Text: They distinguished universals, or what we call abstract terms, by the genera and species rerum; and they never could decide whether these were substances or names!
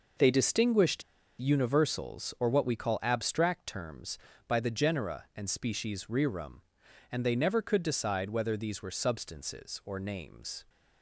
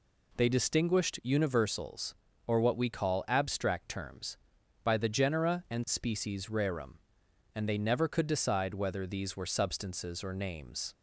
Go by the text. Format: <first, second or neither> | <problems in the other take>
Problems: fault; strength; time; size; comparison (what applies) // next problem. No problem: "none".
second | pauses between "distinguished" and "universals"; at 1.0 s; 0.37 s long